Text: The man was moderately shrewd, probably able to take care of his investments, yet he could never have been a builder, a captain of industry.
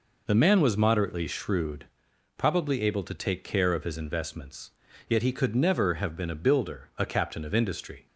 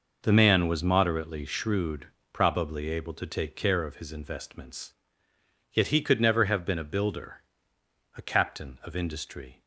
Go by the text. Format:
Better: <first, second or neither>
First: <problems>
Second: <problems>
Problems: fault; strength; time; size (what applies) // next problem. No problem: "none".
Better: neither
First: none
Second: none